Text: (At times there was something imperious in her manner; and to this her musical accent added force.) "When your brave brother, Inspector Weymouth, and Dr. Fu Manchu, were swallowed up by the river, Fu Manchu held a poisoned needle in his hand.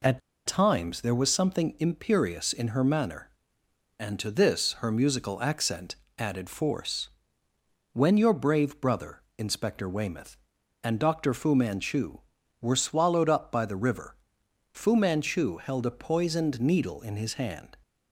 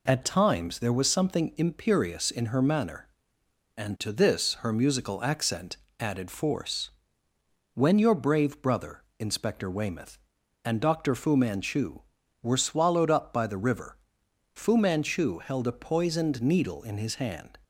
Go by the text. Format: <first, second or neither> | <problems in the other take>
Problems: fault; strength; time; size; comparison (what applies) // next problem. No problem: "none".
second | pauses between "At" and "times"; slight; at 0.2 s; 0.26 s long // pauses between "accent" and "added"; slight; at 5.9 s; 0.24 s long; slight in the second